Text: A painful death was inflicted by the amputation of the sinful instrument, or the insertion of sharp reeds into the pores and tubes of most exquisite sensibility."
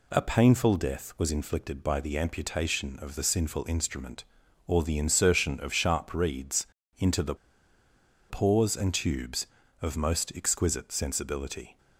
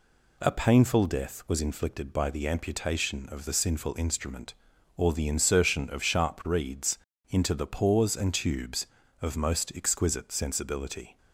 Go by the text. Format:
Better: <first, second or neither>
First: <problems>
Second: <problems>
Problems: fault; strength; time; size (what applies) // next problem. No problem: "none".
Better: second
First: pauses between "reeds" and "into"; slight; at 6.6 s; 0.32 s long // pauses between "the" and "pores"; noticeable; at 7.3 s; 0.93 s long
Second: pauses between "reeds" and "into"; slight; at 6.9 s; 0.32 s long